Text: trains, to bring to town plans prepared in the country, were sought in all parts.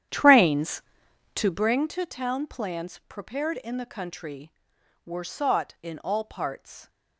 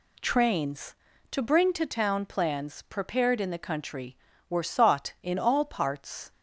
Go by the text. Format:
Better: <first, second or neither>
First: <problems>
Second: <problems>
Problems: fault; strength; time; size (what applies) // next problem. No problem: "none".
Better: second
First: starts louder than the rest; strong; until 1.8 s; 10 dB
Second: none